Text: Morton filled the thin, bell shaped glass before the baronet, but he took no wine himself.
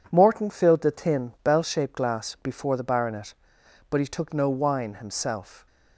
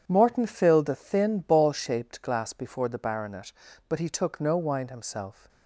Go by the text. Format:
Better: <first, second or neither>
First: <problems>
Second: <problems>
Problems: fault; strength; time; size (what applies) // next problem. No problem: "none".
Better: first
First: none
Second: starts louder than the rest; strong; until 1.0 s; 8 dB // says "ball" for "bell"; at 1.3 s